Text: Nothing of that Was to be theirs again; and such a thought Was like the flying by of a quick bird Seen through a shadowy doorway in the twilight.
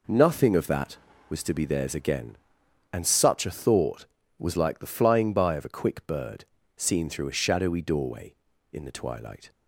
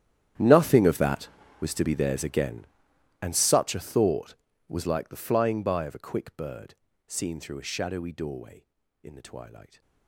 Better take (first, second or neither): first